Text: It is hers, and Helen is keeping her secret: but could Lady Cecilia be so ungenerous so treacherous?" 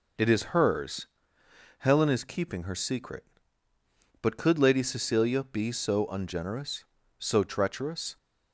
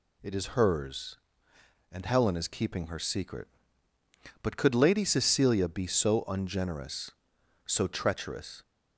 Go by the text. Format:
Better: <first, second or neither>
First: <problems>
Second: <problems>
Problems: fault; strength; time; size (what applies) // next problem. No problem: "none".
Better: second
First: skips "and"; at 1.4 s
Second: none